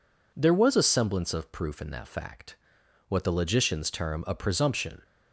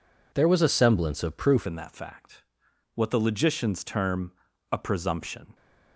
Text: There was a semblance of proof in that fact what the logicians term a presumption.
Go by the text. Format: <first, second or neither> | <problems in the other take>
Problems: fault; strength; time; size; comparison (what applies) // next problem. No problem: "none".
first | changes voice at "in"; from 1.6 s on; 3.9 s long // pauses between "fact" and "what"; noticeable; at 2.4 s; 0.50 s long; noticeable in the first // pauses between "term" and "a"; at 4.3 s; 0.40 s long